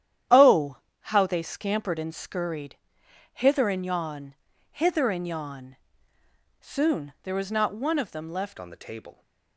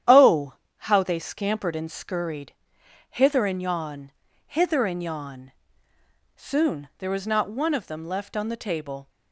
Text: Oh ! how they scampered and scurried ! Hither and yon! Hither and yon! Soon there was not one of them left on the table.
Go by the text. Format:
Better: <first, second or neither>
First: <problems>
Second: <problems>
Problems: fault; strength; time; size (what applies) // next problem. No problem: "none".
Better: second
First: starts louder than the rest; strong; until 1.5 s; 10.5 dB // changes voice at "on"; from 8.5 s on; 0.7 s long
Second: starts louder than the rest; strong; until 1.3 s; 10 dB